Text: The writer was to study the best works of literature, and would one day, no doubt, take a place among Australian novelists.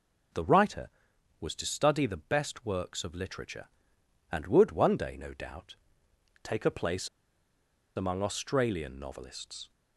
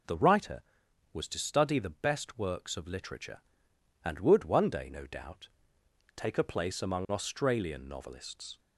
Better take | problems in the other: second | pauses between "place" and "among"; noticeable; at 7.0 s; 0.87 s long

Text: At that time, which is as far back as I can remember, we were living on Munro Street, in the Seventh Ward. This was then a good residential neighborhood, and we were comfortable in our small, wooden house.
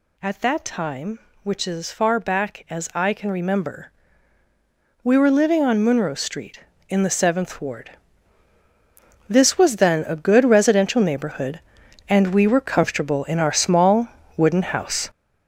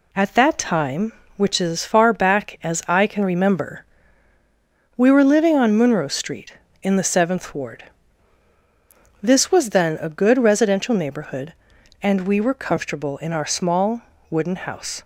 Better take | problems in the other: second | gets louder; strong; throughout; 8 dB

